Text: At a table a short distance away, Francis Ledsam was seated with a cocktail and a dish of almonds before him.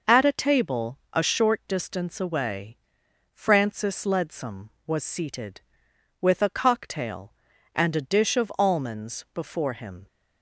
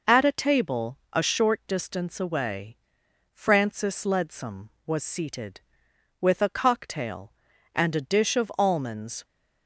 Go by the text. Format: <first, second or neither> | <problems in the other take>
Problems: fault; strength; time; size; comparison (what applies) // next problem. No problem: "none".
first | stops before "before him"; at 9.2 s